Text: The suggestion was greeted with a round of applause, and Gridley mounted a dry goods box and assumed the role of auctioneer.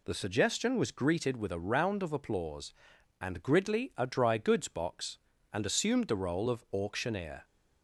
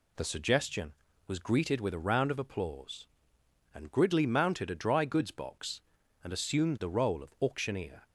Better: second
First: skips "mounted"; at 3.9 s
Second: none

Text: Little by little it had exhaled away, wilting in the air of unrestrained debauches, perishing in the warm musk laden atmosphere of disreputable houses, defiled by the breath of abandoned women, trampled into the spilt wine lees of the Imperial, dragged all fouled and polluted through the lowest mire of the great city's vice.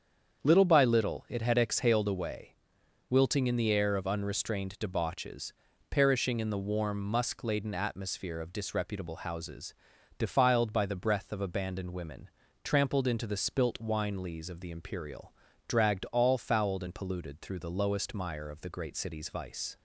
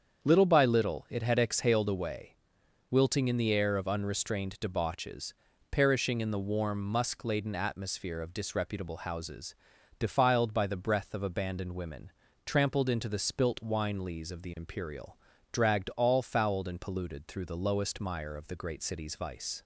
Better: neither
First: starts louder than the rest; strong; until 1.4 s; 7.5 dB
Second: starts louder than the rest; strong; until 1.2 s; 7.5 dB

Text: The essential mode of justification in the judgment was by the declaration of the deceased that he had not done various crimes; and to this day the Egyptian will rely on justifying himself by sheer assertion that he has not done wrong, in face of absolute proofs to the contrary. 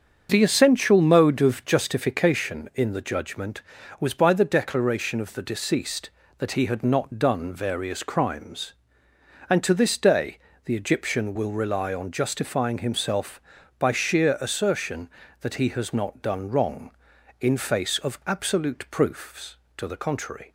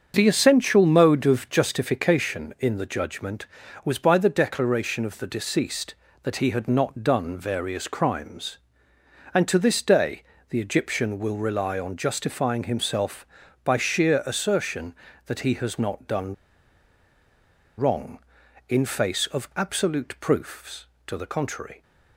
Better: first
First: starts louder than the rest; until 1.3 s; 7 dB // pauses between "day" and "the"; slight; at 10.3 s; 0.28 s long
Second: starts louder than the rest; strong; until 1.1 s; 7 dB // pauses between "day" and "the"; slight; at 10.2 s; 0.28 s long // pauses between "done" and "wrong"; strong; at 16.3 s; 1.4 s long

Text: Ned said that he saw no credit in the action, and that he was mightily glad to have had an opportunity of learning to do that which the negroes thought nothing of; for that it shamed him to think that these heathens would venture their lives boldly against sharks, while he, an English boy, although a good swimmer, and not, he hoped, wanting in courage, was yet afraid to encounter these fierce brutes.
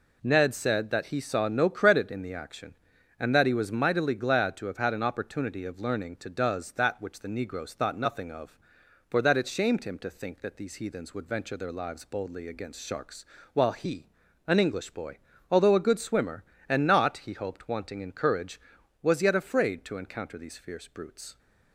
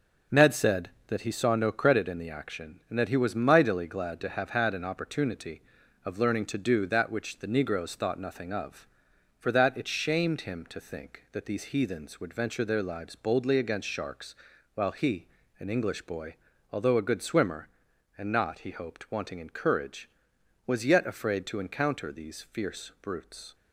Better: second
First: says "does" for "do"; at 6.2 s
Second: none

